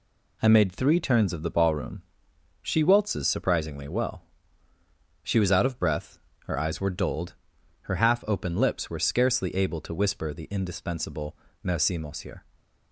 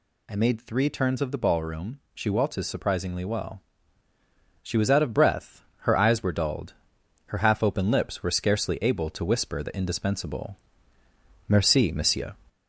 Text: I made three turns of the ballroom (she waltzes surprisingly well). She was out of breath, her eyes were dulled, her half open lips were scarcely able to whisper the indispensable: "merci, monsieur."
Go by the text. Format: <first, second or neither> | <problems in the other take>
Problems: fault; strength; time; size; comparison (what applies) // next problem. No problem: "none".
first | gets louder; slight; throughout; 2.5 dB